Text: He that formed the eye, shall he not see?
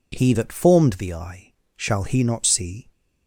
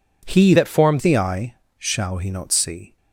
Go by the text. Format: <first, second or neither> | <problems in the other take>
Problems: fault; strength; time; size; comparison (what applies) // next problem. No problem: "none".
first | changes voice from "that" to "formed"; from 0.5 to 1.0 s; 0.5 s long